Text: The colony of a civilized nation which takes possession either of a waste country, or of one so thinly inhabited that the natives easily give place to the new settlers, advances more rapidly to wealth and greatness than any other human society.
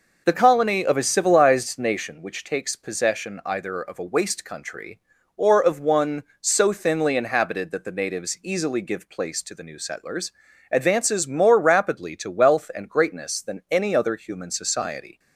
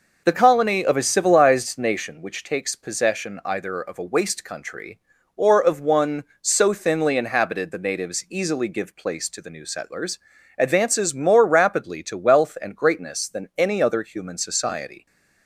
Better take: first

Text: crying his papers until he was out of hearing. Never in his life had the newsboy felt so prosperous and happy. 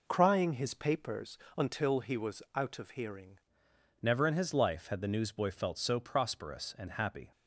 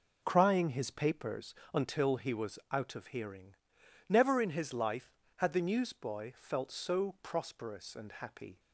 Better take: second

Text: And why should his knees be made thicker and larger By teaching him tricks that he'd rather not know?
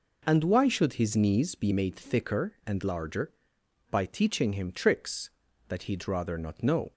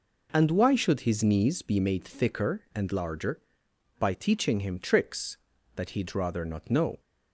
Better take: neither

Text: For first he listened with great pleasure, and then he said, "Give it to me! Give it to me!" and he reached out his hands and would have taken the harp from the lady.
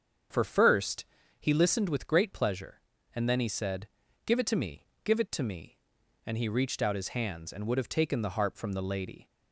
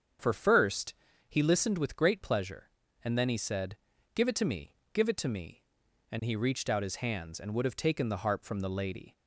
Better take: neither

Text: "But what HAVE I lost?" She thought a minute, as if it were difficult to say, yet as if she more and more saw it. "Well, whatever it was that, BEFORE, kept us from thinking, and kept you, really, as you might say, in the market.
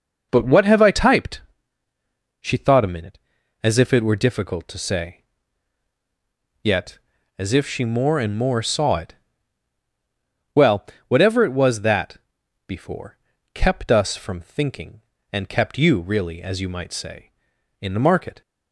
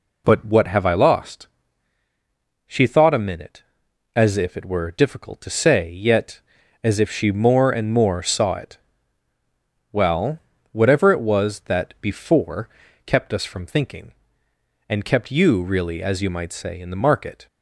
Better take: second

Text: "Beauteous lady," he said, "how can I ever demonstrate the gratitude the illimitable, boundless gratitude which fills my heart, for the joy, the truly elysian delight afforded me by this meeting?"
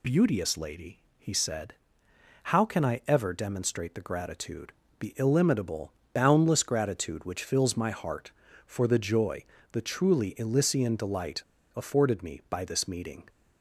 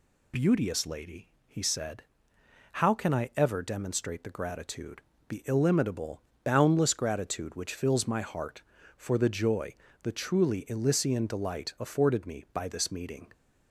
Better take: second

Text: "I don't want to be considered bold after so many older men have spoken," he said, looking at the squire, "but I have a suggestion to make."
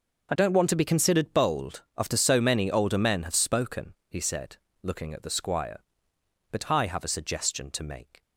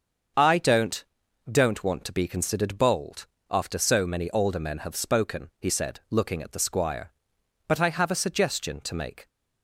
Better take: first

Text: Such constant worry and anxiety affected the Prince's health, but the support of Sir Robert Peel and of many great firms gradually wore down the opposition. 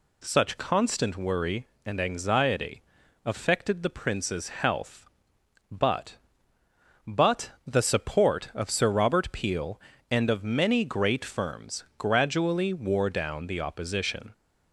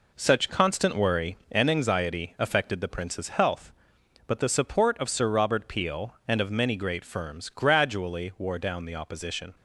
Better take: second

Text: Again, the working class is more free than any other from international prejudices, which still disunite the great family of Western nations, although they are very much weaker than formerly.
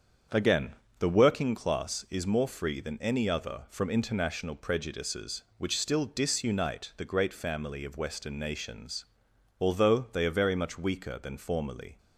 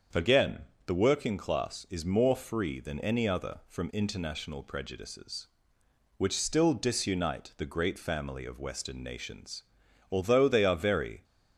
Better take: first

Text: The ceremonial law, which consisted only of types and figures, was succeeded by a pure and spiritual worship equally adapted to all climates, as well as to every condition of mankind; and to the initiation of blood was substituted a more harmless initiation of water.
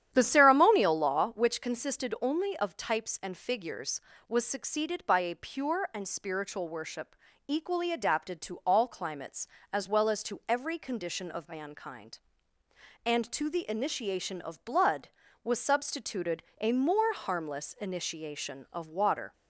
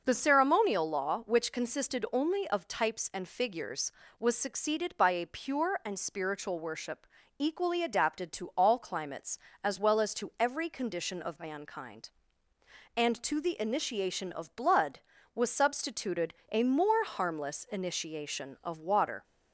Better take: second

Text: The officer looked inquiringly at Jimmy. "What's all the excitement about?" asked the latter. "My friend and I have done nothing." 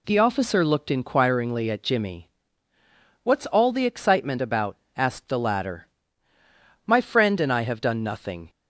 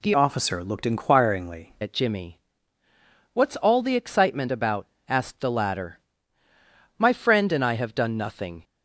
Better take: first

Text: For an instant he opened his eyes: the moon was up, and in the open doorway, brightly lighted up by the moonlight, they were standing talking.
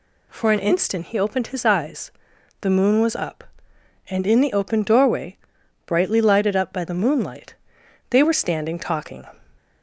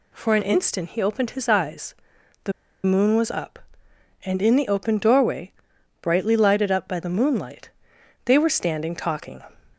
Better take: first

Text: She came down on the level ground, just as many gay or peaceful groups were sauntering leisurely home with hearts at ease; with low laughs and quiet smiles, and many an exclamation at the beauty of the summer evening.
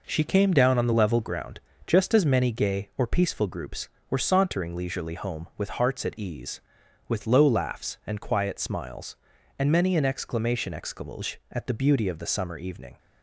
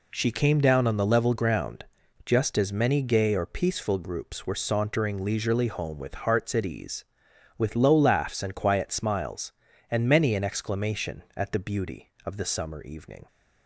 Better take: second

